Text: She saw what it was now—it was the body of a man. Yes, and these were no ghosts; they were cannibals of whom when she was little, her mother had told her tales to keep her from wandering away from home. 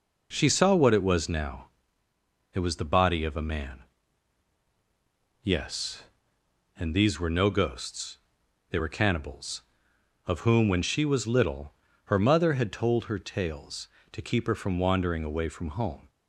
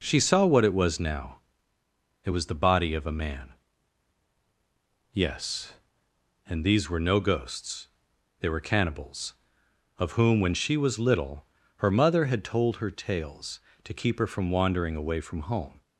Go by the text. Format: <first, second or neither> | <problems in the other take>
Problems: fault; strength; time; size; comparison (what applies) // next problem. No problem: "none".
neither | none